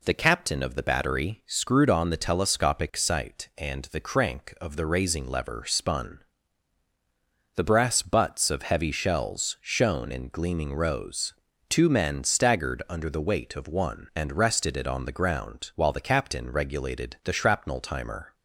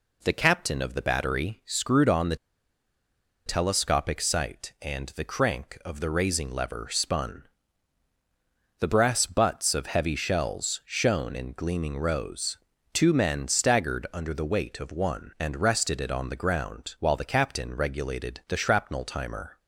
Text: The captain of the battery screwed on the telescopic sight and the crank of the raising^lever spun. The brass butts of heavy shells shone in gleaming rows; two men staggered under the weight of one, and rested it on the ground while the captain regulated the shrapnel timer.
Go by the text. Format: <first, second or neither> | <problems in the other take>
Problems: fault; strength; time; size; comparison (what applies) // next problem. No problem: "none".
first | pauses between "the" and "telescopic"; at 2.3 s; 1.0 s long